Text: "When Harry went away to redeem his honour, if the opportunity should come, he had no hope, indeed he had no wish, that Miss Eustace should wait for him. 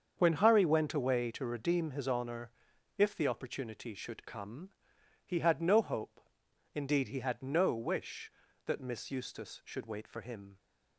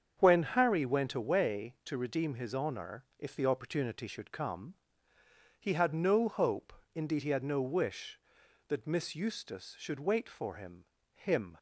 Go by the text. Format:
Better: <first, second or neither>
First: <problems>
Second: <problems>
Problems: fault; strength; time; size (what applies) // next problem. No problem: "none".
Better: first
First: starts louder than the rest; until 1.1 s; 7 dB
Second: starts louder than the rest; strong; until 1.1 s; 7.5 dB // says "him" twice; at 11.1 s